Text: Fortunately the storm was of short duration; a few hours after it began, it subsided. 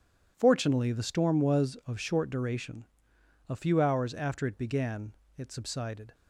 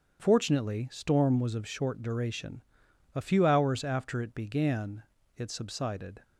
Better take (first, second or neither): first